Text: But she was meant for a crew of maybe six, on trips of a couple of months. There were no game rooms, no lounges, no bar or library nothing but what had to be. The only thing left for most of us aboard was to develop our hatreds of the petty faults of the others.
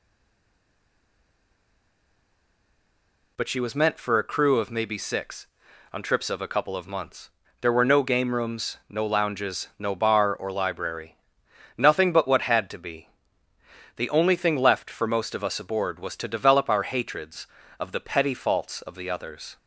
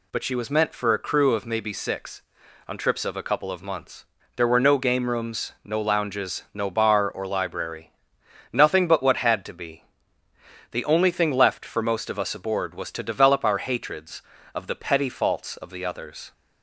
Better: second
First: stays silent before the first word; strong; until 3.3 s; 3.3 s long // pauses between "library" and "nothing"; noticeable; at 11.1 s; 0.58 s long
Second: pauses between "library" and "nothing"; noticeable; at 7.9 s; 0.58 s long

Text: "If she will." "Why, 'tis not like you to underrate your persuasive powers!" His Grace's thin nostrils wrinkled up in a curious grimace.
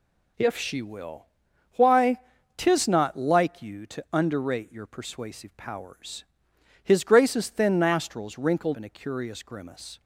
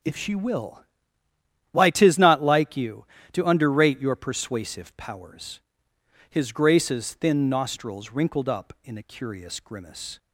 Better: second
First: skips "up"; at 8.7 s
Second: none

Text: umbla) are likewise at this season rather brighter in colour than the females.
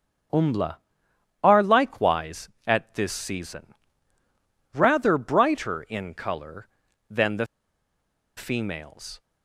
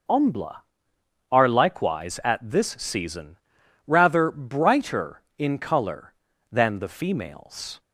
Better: second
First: starts louder than the rest; strong; until 1.9 s; 7.5 dB // pauses between "season" and "rather"; at 3.6 s; 1.0 s long // pauses between "the" and "females"; noticeable; at 7.4 s; 0.90 s long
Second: pauses between "season" and "rather"; noticeable; at 3.3 s; 0.50 s long

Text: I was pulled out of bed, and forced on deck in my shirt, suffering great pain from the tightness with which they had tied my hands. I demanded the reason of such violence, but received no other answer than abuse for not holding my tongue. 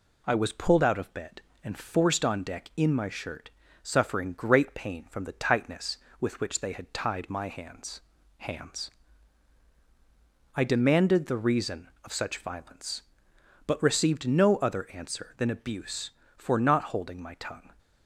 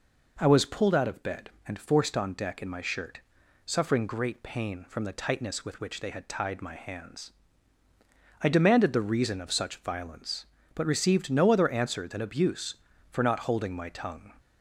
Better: second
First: says "hands" twice; at 8.3 s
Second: none

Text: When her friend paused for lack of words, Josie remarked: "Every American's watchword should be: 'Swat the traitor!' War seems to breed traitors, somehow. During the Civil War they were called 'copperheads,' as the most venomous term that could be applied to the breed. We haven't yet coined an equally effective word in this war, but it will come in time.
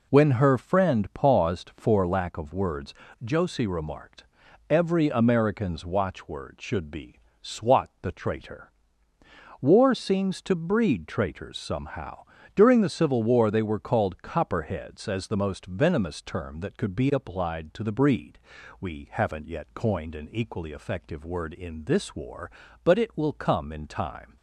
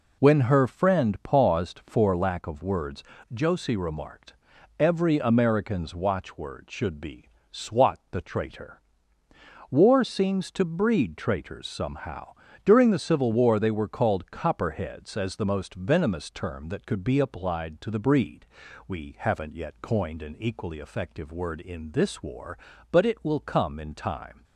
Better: neither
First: none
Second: none

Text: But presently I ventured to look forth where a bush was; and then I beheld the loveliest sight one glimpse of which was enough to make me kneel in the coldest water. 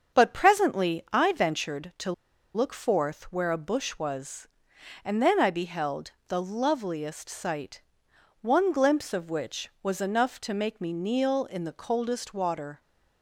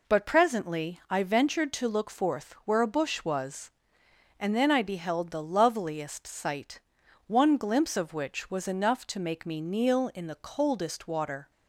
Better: second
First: starts louder than the rest; until 1.2 s; 7 dB // pauses between "to" and "look"; at 2.1 s; 0.41 s long // pauses between "beheld" and "the"; slight; at 6.1 s; 0.18 s long // pauses between "sight" and "one"; noticeable; at 7.8 s; 0.62 s long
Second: pauses between "sight" and "one"; noticeable; at 6.7 s; 0.48 s long

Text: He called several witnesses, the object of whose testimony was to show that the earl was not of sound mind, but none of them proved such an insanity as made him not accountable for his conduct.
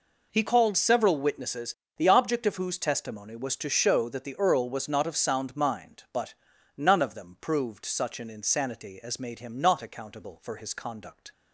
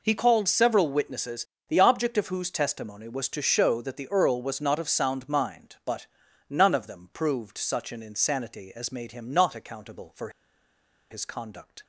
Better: first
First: pauses between "but" and "none"; at 6.3 s; 0.42 s long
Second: pauses between "but" and "none"; at 6.0 s; 0.42 s long // pauses between "for" and "his"; noticeable; at 10.2 s; 0.81 s long

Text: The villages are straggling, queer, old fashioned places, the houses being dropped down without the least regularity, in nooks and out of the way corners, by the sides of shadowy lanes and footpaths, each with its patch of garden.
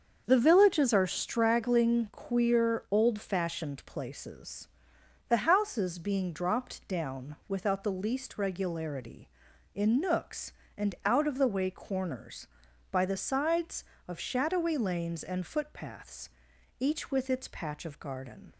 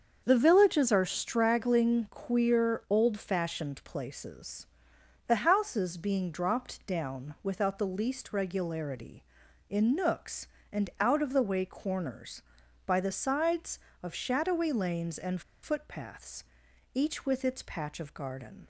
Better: first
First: starts louder than the rest; until 1.3 s; 6.5 dB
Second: starts louder than the rest; until 1.2 s; 6.5 dB // pauses between "and" and "footpaths"; slight; at 15.4 s; 0.21 s long

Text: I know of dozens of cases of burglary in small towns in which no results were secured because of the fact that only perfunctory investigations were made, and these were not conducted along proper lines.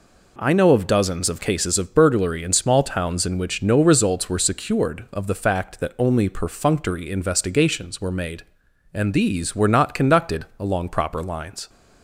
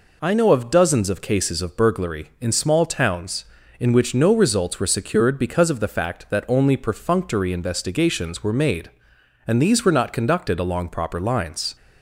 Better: second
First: skips "because"; at 5.0 s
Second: none

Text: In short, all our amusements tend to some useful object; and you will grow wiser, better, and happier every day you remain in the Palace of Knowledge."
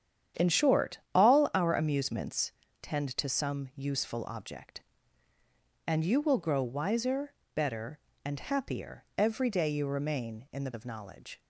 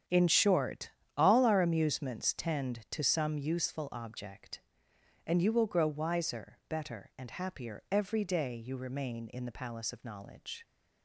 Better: second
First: starts louder than the rest; strong; until 1.5 s; 9 dB // pauses between "amusements" and "tend"; slight; at 2.5 s; 0.30 s long // skips "Palace"; at 10.7 s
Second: starts louder than the rest; strong; until 1.3 s; 8.5 dB

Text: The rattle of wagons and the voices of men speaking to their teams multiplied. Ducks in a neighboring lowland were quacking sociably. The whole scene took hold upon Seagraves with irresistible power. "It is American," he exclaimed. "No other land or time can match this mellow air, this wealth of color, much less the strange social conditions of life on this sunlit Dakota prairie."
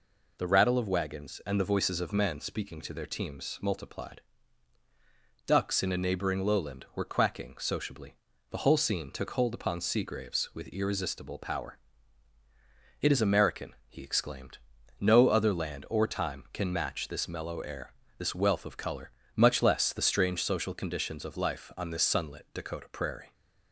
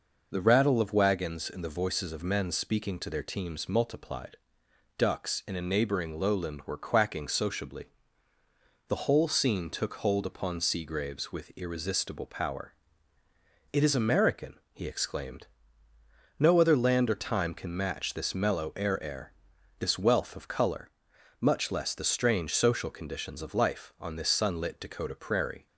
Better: first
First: none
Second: says "air" twice; at 19.0 s

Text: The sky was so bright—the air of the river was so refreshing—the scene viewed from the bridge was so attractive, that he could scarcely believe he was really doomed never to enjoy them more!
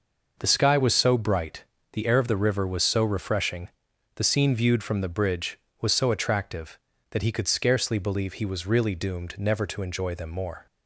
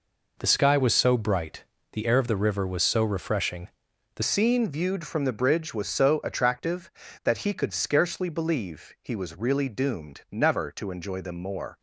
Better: first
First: none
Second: changes voice at "scene"; from 4.2 s on; 7.5 s long

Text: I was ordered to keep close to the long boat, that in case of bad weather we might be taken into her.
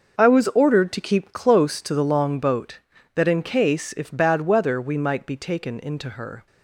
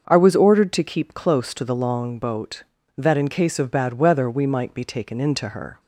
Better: second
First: starts louder than the rest; noticeable; until 1.2 s; 6 dB // says "if" for "of"; at 3.9 s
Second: starts louder than the rest; until 1.1 s; 6.5 dB

